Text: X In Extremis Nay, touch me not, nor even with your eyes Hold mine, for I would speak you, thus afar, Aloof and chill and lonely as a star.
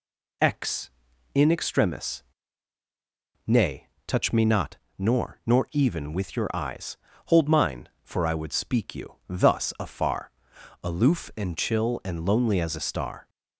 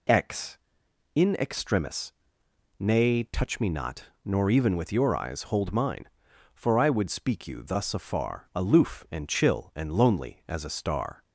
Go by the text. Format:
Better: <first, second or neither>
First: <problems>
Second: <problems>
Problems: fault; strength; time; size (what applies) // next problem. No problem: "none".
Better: second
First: pauses between "Extremis" and "Nay"; at 2.2 s; 1.2 s long // says "nor" twice; at 5.4 s // pauses between "eyes" and "Hold"; slight; at 6.9 s; 0.30 s long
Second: pauses between "Extremis" and "Nay"; noticeable; at 2.1 s; 0.64 s long